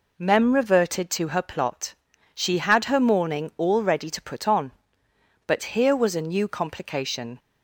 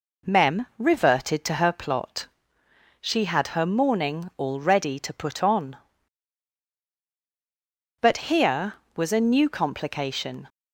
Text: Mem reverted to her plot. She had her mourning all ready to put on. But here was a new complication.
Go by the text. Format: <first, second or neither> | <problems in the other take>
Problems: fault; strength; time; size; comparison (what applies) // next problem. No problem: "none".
neither | none